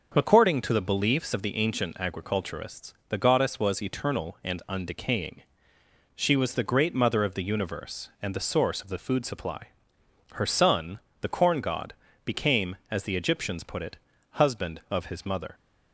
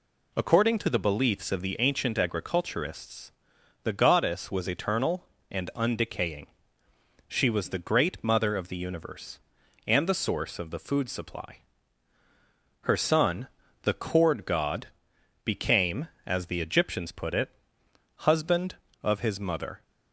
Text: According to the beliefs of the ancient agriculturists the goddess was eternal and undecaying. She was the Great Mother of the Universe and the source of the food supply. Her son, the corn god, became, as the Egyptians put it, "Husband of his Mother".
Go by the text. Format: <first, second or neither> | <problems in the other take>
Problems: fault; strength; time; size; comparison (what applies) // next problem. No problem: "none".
first | pauses between "agriculturists" and "the"; noticeable; at 3.3 s; 0.52 s long // says "cord" for "corn"; at 13.9 s